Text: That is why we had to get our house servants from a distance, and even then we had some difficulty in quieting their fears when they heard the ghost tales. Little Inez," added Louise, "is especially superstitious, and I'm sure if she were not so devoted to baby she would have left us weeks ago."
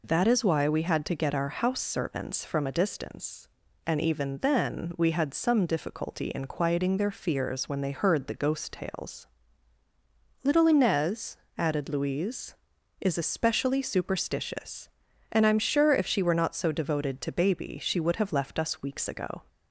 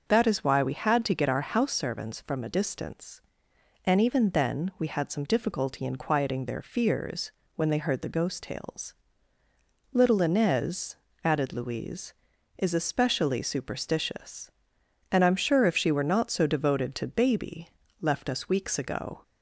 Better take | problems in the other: first | pauses between "fears" and "when"; slight; at 7.3 s; 0.26 s long // skips "she would have"; at 17.8 s

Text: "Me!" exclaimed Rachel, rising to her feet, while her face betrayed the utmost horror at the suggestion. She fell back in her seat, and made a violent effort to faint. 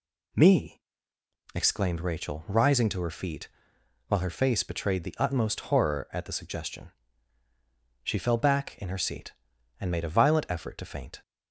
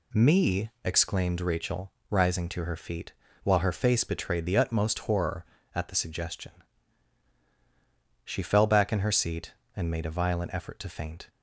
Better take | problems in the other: neither | none

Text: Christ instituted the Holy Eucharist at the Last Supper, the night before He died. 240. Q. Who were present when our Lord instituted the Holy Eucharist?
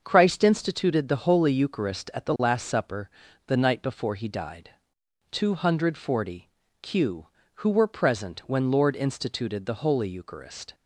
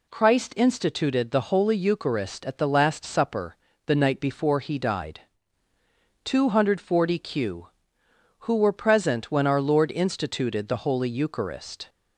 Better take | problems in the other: second | starts louder than the rest; until 1.0 s; 6.5 dB // skips "our"; at 8.7 s

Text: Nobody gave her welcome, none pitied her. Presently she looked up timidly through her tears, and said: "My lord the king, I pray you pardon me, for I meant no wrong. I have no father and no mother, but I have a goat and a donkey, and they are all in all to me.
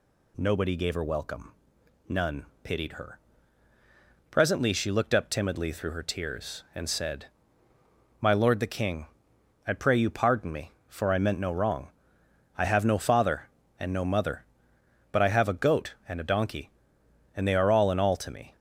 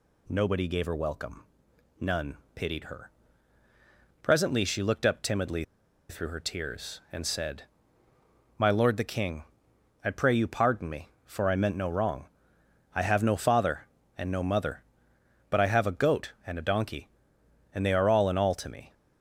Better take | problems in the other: first | pauses between "none" and "pitied"; slight; at 2.3 s; 0.18 s long; slight in the first // pauses between "timidly" and "through"; noticeable; at 5.6 s; 0.46 s long

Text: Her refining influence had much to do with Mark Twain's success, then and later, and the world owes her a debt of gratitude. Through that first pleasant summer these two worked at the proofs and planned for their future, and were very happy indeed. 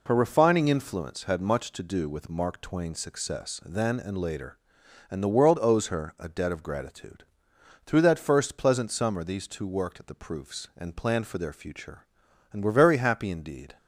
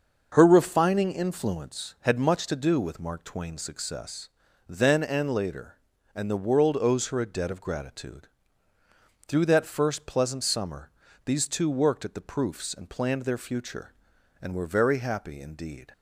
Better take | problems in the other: first | starts louder than the rest; until 1.3 s; 6.5 dB // pauses between "summer" and "these"; slight; at 10.8 s; 0.36 s long // skips "for"; at 13.2 s

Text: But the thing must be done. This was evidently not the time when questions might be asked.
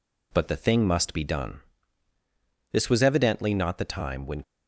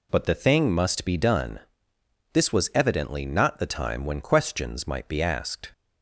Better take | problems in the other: second | stops before "questions might be asked"; at 4.4 s

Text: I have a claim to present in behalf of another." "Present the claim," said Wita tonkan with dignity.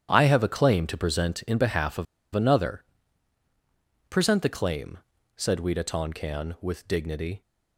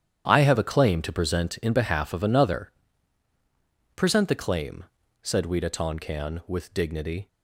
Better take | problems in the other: second | starts louder than the rest; strong; until 1.1 s; 10 dB; strong in the second // pauses between "of" and "another"; slight; at 2.0 s; 0.29 s long

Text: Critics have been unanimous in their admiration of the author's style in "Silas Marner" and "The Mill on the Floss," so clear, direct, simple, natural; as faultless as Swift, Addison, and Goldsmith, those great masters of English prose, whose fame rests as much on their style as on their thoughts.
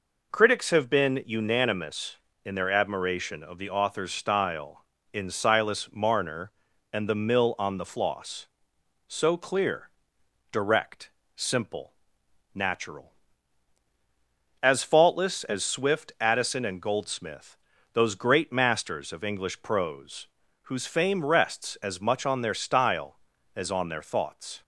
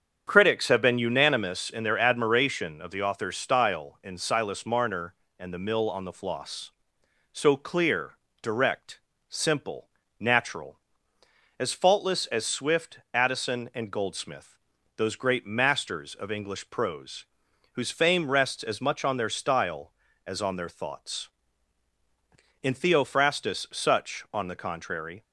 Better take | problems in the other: first | starts louder than the rest; strong; until 1.2 s; 8 dB // goes on to say "In Theophrastus Such on the contrary"; strong; from 22.6 s on; 2.6 s long

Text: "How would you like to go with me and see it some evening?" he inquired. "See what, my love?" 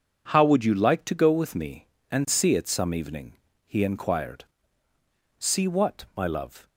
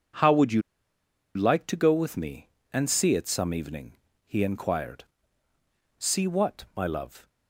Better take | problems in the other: first | pauses between "you" and "like"; noticeable; at 0.6 s; 0.74 s long

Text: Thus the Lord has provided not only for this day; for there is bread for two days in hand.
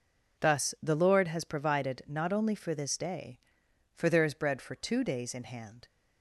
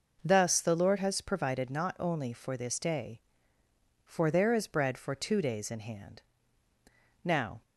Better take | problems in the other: first | goes on to say "Now"; slight; from 7.2 s on; 0.38 s long

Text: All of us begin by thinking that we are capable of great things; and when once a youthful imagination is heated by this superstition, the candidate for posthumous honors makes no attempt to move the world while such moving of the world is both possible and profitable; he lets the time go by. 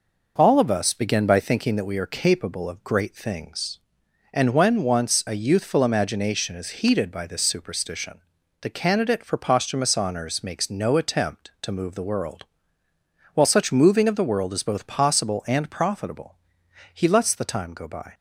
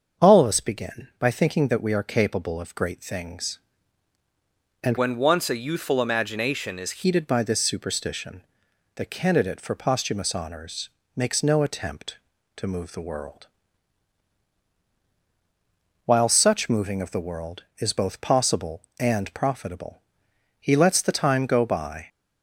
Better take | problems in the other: first | starts louder than the rest; until 1.3 s; 6.5 dB // changes voice from "when" to "is"; from 4.9 to 7.0 s; 2.1 s long // pauses between "honors" and "makes"; slight; at 10.8 s; 0.26 s long // pauses between "world" and "while"; strong; at 13.4 s; 2.6 s long; noticeable in the first

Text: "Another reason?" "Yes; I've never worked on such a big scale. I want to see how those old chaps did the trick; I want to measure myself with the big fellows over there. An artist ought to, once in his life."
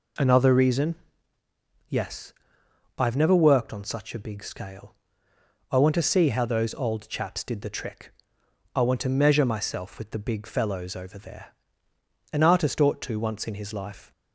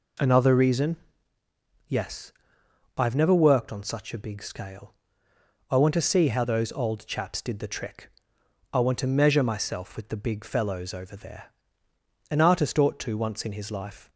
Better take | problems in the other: neither | none

